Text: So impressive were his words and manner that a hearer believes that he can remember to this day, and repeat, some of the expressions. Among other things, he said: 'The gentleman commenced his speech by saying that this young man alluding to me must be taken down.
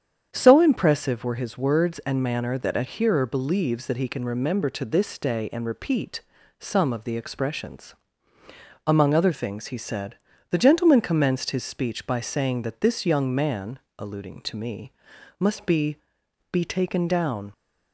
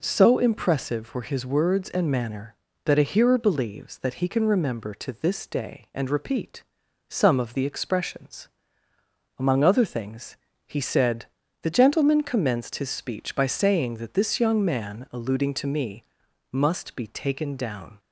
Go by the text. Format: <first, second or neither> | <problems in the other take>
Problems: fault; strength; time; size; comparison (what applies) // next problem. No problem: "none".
second | starts louder than the rest; strong; until 1.3 s; 8 dB // pauses between "man" and "alluding"; slight; at 13.7 s; 0.20 s long // pauses between "me" and "must"; at 14.9 s; 0.44 s long; noticeable in the second // says "be" twice; at 16.5 s